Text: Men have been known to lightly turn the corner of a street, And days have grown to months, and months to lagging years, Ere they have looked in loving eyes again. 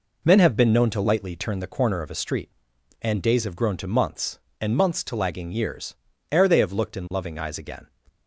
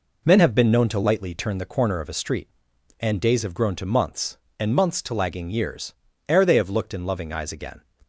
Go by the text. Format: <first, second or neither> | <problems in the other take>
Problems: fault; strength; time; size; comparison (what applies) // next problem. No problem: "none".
neither | none